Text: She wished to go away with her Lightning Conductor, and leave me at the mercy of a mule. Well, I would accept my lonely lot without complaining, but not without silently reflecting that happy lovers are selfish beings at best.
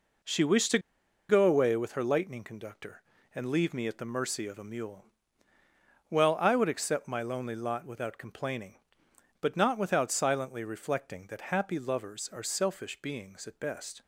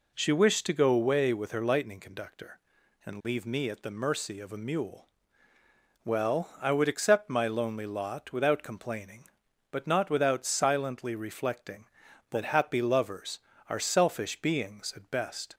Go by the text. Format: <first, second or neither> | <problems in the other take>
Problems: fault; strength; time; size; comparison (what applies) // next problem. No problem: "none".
second | pauses between "to" and "go"; noticeable; at 0.7 s; 0.51 s long